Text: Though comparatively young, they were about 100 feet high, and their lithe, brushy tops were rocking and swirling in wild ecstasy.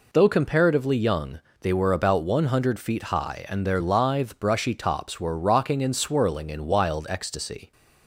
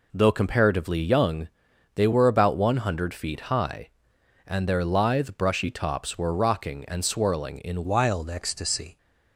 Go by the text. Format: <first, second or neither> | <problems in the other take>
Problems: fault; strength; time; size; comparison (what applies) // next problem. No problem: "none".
first | changes voice at "wild"; from 7.8 s on; 1.1 s long